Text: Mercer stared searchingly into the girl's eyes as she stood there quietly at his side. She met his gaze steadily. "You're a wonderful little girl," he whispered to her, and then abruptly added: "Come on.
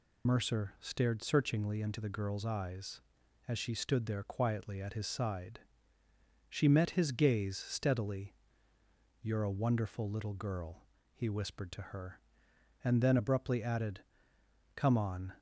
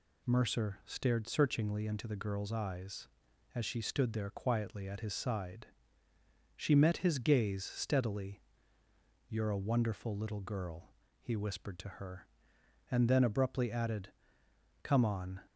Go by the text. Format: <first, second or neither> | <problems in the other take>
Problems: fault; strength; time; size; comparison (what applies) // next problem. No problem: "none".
second | loses the start of "Mercer"; at 0.2 s; 55 ms